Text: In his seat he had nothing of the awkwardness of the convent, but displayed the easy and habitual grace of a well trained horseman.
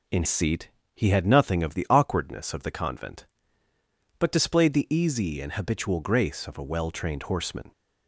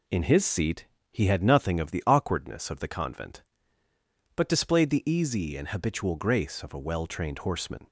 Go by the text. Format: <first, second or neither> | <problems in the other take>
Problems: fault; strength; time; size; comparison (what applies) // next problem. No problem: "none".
second | skips "his"; at 0.2 s // pauses between "seat" and "he"; slight; at 0.6 s; 0.24 s long; slight in the second